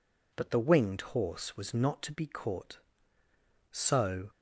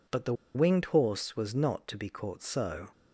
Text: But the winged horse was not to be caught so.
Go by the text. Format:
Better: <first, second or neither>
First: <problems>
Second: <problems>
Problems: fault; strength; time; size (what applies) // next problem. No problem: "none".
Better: first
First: none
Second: pauses between "the" and "winged"; slight; at 0.3 s; 0.21 s long